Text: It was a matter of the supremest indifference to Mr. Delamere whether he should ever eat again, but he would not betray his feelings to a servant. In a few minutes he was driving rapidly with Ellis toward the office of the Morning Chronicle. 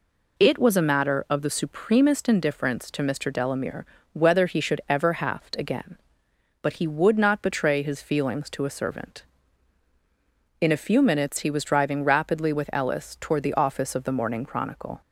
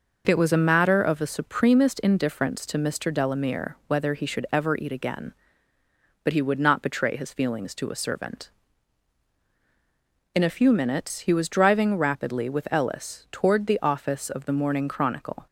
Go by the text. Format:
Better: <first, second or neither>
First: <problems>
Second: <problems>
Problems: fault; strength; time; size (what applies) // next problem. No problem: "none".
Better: second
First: pauses between "Delamere" and "whether"; slight; at 3.8 s; 0.26 s long // says "haft" for "eat"; at 5.1 s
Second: none